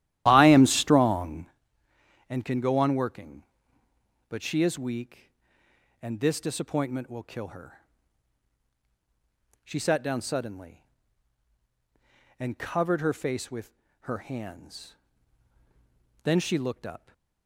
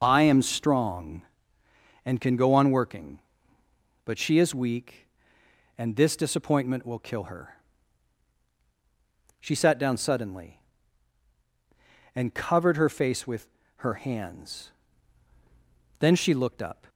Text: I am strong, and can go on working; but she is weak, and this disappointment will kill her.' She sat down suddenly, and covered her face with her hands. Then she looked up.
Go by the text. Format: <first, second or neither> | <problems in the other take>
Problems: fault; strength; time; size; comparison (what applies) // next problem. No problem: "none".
second | starts louder than the rest; strong; until 1.5 s; 13 dB // pauses between "with" and "her"; slight; at 13.7 s; 0.30 s long; slight in the second